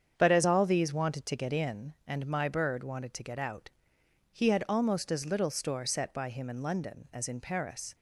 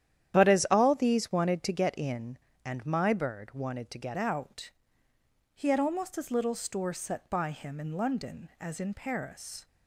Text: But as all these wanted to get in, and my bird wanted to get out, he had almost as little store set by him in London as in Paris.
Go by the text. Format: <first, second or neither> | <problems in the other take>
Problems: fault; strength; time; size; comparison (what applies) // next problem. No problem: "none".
first | starts louder than the rest; strong; until 1.4 s; 10.5 dB; strong in the first // changes voice at "out"; from 4.1 s on; 5.5 s long